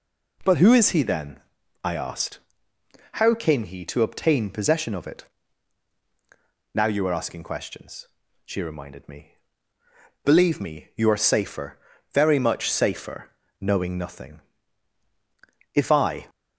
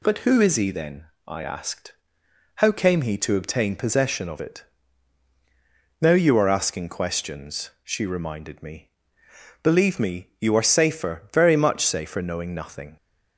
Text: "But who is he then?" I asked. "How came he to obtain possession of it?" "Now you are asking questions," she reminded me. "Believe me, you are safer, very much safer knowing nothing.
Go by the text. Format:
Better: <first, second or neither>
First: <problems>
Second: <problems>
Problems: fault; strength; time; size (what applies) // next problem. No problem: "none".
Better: second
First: pauses between "safer" and "knowing"; slight; at 13.3 s; 0.28 s long // goes on to say "If I"; from 15.7 s on; 0.54 s long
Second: none